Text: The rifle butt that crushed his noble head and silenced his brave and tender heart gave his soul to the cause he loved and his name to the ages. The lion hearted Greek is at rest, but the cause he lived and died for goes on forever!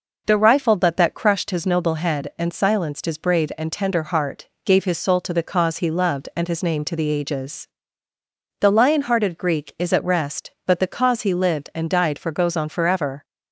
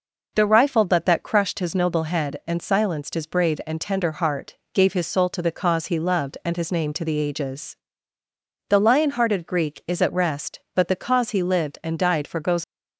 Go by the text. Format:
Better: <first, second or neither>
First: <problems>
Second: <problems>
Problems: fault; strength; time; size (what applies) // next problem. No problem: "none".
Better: first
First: pauses between "heart" and "gave"; slight; at 4.4 s; 0.16 s long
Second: pauses between "heart" and "gave"; slight; at 4.5 s; 0.16 s long // stops before "on forever"; at 12.6 s